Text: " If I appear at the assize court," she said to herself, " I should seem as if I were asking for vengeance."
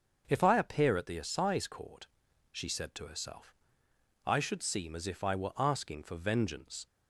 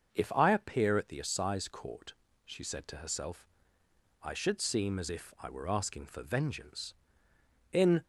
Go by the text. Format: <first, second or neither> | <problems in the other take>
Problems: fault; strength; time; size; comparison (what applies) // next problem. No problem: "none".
first | starts louder than the rest; until 1.1 s; 6.5 dB // goes on to say "In"; slight; from 7.7 s on; 0.32 s long